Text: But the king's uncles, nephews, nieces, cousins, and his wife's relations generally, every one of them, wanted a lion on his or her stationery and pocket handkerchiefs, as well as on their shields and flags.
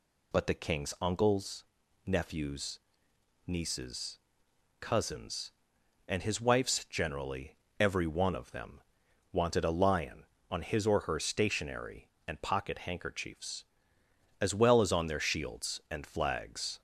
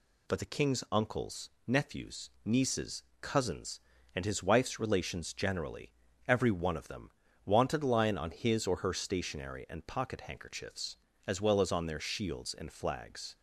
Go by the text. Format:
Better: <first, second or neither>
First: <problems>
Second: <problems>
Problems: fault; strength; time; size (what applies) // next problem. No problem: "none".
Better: second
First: skips "relations"; at 6.8 s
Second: none